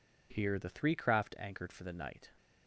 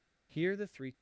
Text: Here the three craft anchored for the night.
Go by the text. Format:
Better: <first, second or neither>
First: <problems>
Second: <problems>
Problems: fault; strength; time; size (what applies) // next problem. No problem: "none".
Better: first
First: none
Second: stops before "craft anchored for the night"; at 0.9 s